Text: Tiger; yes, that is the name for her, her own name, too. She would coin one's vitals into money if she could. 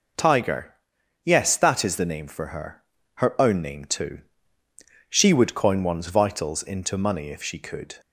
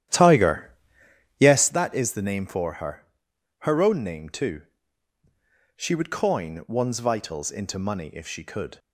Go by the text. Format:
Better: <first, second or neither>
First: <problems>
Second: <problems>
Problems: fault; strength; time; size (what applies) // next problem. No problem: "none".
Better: first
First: none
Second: starts louder than the rest; strong; until 1.8 s; 11 dB